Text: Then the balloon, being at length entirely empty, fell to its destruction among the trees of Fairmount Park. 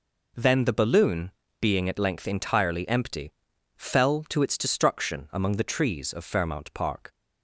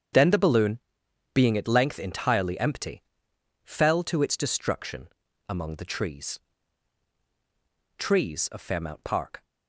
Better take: first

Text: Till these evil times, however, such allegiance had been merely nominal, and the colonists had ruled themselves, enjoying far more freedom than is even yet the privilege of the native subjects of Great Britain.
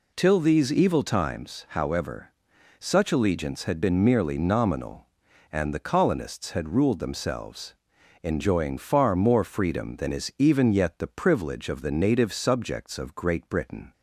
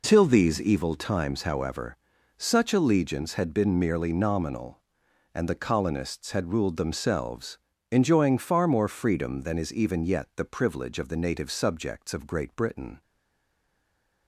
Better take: first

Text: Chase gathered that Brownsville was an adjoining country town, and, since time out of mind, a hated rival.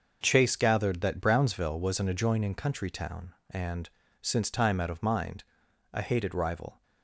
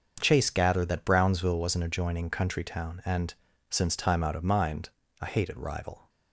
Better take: neither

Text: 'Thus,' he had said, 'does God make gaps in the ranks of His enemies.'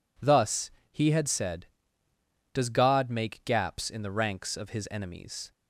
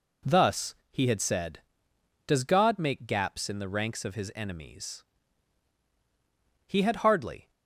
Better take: first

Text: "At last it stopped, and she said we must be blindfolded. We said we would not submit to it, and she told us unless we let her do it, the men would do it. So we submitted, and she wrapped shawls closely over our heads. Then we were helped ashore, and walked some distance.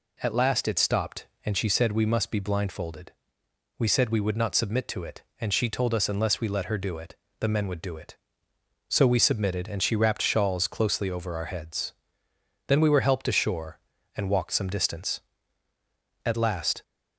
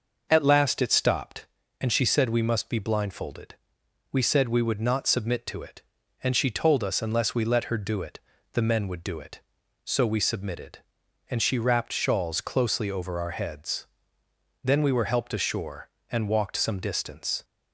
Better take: second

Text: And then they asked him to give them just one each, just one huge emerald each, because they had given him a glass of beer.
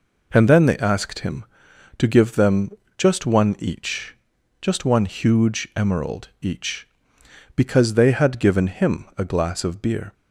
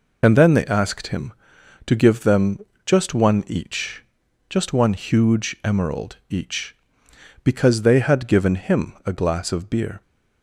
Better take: first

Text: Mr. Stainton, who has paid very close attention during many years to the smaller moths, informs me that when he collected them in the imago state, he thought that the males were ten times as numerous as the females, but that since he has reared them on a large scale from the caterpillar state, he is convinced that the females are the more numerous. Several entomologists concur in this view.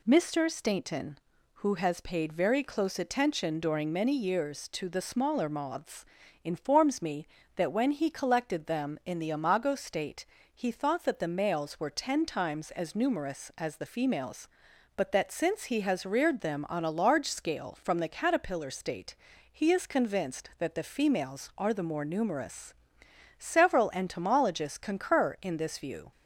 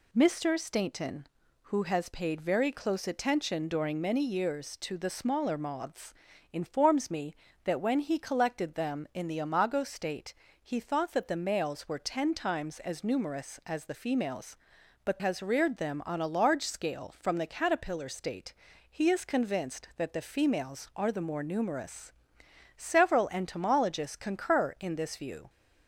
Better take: first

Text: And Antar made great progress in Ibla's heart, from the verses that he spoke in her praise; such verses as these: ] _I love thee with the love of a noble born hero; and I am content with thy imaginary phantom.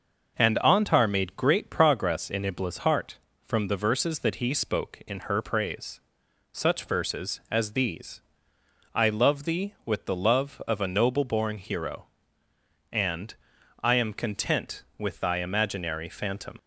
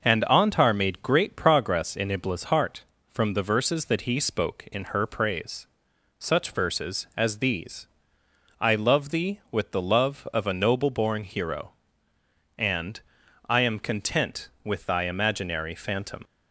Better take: neither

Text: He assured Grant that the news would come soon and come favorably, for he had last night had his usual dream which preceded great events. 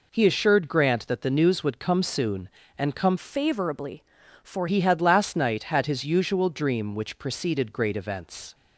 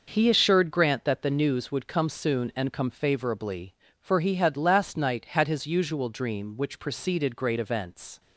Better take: second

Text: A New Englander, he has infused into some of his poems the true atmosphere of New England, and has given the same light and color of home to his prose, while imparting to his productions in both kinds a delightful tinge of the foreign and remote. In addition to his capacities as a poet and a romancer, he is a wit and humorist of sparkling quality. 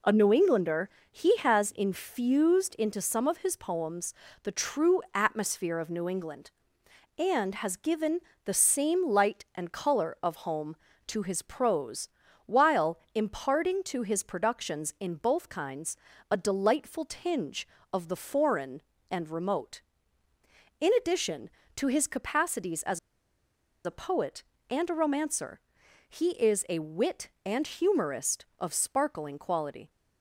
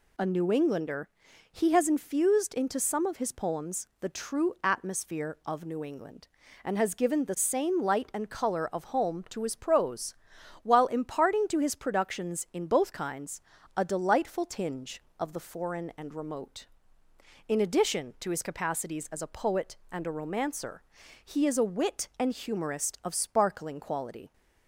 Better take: second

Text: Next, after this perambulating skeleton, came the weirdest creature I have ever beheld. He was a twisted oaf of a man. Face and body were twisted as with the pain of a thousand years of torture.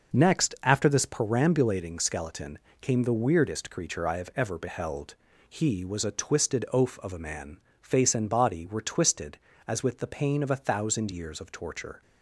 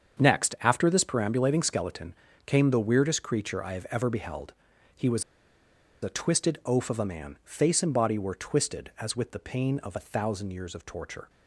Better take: first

